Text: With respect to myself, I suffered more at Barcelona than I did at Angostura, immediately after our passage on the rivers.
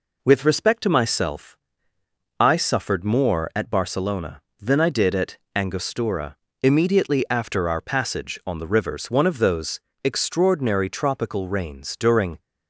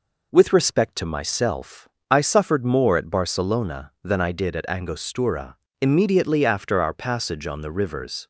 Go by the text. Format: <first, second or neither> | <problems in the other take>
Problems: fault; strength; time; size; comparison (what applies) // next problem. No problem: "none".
second | pauses between "at" and "Angostura"; slight; at 5.3 s; 0.18 s long // goes on to say "One of those extraordinary tropical rains during"; strong; from 9.0 s on; 3.3 s long